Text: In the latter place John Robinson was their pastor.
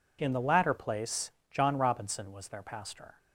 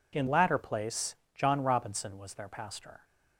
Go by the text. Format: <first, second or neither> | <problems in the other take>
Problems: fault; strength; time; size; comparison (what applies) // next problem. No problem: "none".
first | skips "the"; at 0.2 s // pauses between "place" and "John"; slight; at 1.1 s; 0.20 s long; slight in the first